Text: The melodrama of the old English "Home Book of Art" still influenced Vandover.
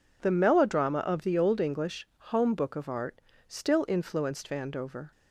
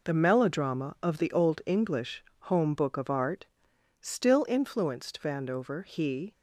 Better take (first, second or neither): first